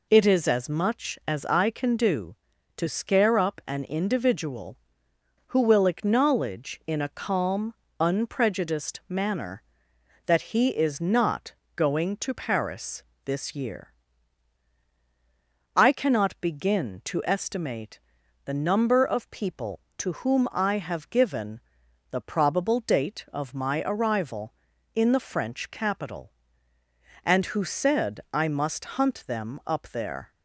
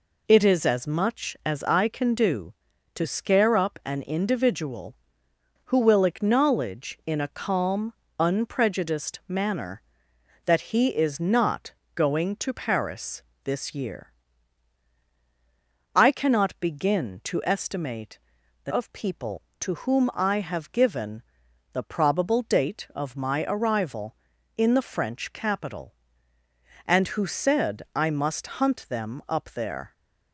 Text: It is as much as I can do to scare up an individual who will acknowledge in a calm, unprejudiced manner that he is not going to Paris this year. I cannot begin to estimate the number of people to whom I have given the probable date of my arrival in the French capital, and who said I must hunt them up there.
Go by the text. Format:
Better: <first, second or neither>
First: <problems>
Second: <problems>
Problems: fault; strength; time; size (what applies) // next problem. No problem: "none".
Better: first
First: pauses between "not" and "going"; slight; at 11.5 s; 0.20 s long // pauses between "Paris" and "this"; slight; at 13.0 s; 0.22 s long // pauses between "estimate" and "the"; noticeable; at 17.9 s; 0.46 s long // pauses between "given" and "the"; noticeable; at 21.5 s; 0.52 s long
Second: pauses between "not" and "going"; slight; at 11.7 s; 0.20 s long // pauses between "Paris" and "this"; slight; at 13.2 s; 0.22 s long // pauses between "estimate" and "the"; noticeable; at 18.1 s; 0.46 s long // skips "number"; at 18.7 s // pauses between "given" and "the"; noticeable; at 21.2 s; 0.52 s long